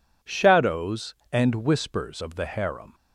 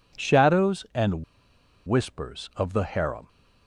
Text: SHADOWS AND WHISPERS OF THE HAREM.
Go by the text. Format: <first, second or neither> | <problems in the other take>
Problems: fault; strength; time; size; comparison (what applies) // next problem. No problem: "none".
first | pauses between "AND" and "WHISPERS"; noticeable; at 1.2 s; 0.63 s long